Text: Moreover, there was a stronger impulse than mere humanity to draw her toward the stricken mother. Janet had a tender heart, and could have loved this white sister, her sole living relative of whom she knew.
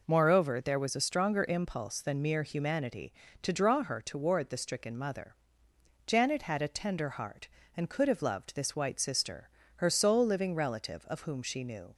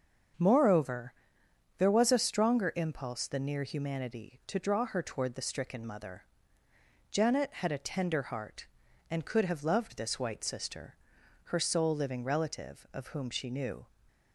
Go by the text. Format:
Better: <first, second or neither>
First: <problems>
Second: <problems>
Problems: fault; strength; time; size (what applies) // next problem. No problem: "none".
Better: first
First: none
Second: starts louder than the rest; until 2.0 s; 7 dB // says "near" for "mere"; at 3.4 s